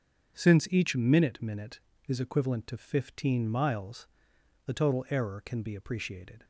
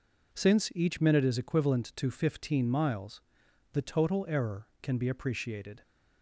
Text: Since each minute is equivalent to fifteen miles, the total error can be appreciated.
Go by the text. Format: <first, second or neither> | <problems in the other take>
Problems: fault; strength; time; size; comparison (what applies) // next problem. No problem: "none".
second | starts louder than the rest; strong; until 1.4 s; 7.5 dB // says "minute" twice; at 1.4 s